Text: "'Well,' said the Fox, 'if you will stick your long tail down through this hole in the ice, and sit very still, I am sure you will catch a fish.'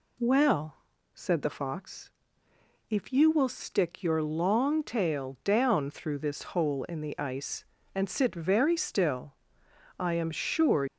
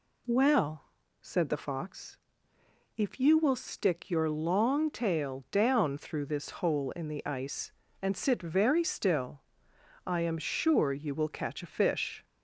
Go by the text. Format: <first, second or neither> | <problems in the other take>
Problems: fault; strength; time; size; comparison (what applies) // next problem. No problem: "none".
second | stops before "you will catch a fish"; at 10.8 s